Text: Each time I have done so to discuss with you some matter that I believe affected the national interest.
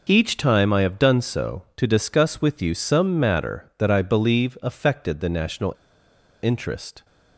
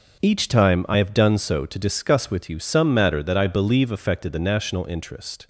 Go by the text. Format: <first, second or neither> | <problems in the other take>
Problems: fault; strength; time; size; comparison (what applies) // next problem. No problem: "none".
second | pauses between "national" and "interest"; noticeable; at 5.7 s; 0.69 s long